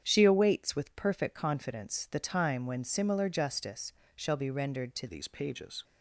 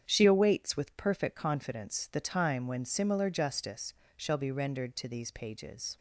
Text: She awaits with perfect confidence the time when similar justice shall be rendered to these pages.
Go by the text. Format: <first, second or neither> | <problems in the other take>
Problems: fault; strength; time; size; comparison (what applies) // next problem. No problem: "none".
second | starts louder than the rest; strong; until 1.0 s; 8 dB; strong in the second // pauses between "justice" and "shall"; slight; at 3.9 s; 0.22 s long; slight in the second // changes voice at "these"; from 5.0 s on; 0.8 s long